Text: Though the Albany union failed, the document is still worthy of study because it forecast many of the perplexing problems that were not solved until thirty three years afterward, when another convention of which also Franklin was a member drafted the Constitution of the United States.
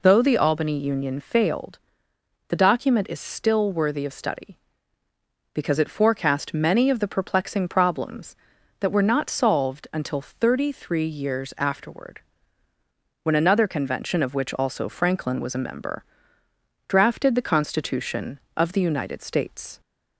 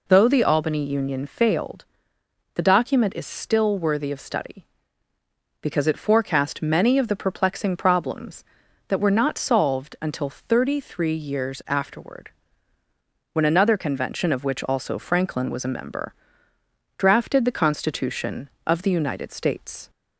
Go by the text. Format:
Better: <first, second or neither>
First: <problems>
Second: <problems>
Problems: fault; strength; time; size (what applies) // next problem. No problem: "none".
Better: neither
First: pauses between "member" and "drafted"; noticeable; at 16.0 s; 0.84 s long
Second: pauses between "member" and "drafted"; noticeable; at 16.1 s; 0.84 s long